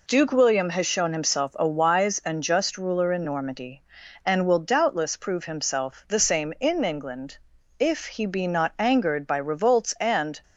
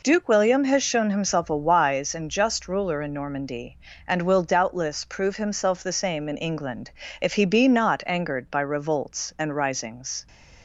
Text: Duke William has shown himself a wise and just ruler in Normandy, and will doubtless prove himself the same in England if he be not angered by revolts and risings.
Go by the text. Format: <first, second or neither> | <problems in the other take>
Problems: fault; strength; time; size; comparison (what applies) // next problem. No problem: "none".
second | pauses between "England" and "if"; at 7.3 s; 0.40 s long; slight in the second // stops before "risings"; at 10.4 s